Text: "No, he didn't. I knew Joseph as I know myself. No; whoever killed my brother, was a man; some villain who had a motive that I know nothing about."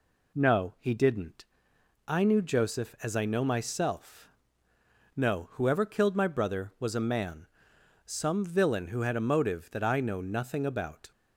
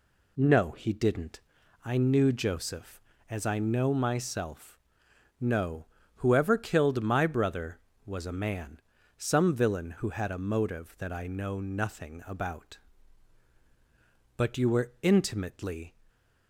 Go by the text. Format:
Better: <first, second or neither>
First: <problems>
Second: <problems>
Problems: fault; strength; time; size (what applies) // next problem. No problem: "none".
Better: first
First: none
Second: goes on to say "But you were intimately"; from 14.3 s on; 1.5 s long